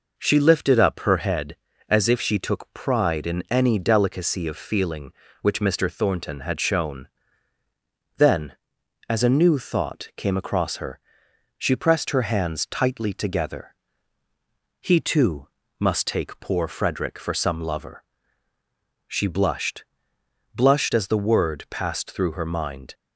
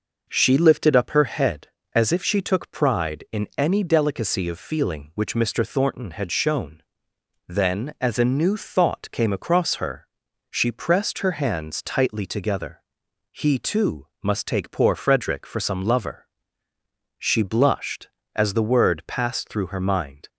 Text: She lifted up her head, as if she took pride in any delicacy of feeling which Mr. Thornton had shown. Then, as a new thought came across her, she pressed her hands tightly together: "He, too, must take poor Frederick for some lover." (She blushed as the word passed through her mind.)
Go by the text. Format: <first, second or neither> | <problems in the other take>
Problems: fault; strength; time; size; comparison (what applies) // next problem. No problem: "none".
second | says "blushed" twice; at 20.5 s